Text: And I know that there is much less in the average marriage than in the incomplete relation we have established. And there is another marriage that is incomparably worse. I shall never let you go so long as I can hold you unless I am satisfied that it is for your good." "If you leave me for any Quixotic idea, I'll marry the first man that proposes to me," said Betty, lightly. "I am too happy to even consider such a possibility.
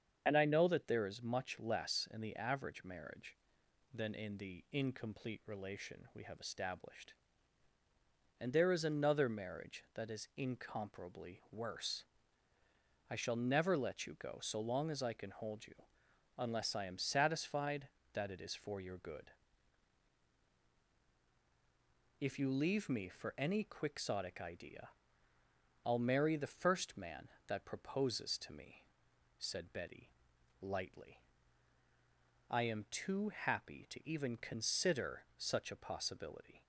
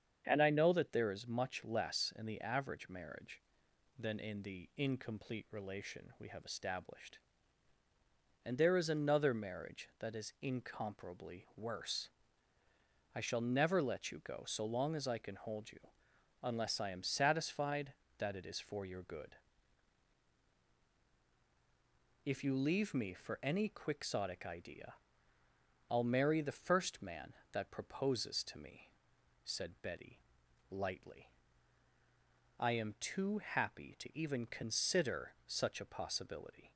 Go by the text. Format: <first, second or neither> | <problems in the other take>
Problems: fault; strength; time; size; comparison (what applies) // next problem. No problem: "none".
second | loses the start of "And"; at 0.2 s; 60 ms // starts louder than the rest; strong; until 1.2 s; 7.5 dB; strong in the second // pauses between "you" and "unless"; noticeable; at 15.7 s; 0.64 s long; noticeable in the second